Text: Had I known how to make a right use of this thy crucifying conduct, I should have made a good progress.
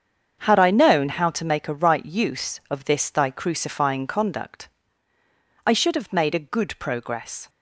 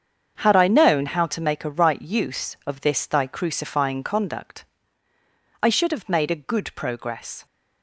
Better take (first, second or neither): neither